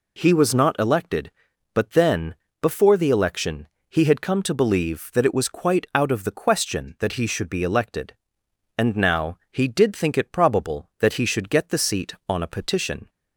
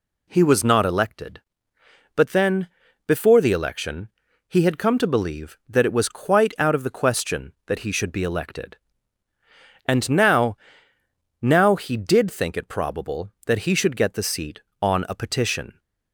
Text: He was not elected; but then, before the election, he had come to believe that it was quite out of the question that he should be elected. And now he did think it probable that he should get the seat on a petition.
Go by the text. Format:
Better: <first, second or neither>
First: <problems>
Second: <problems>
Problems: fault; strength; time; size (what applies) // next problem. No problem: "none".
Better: first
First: none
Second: says "now" twice; at 11.4 s